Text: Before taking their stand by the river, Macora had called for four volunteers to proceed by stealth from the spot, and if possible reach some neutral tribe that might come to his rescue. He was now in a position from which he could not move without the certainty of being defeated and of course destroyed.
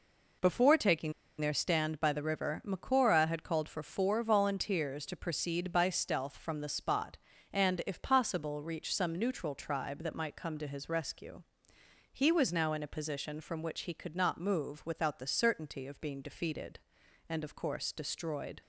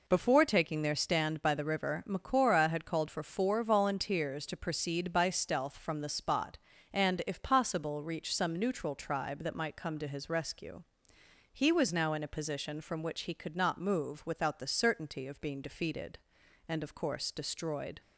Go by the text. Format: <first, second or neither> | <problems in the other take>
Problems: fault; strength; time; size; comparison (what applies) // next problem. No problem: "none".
second | pauses between "taking" and "their"; slight; at 1.1 s; 0.28 s long